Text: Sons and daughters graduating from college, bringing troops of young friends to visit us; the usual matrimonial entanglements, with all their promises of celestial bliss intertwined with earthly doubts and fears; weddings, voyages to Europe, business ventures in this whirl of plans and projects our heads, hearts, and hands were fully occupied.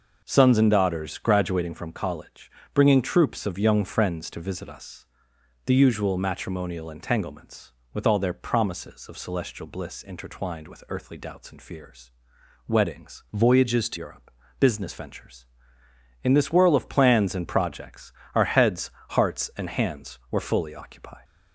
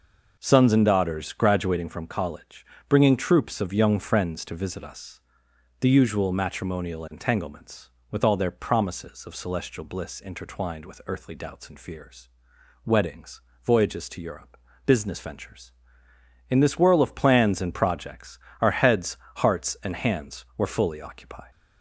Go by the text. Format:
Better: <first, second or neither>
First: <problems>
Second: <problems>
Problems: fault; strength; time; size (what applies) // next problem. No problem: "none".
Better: second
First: changes voice from "voyages" to "to"; from 13.3 to 13.9 s; 0.6 s long // pauses between "projects" and "our"; slight; at 18.1 s; 0.24 s long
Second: pauses between "projects" and "our"; slight; at 18.3 s; 0.24 s long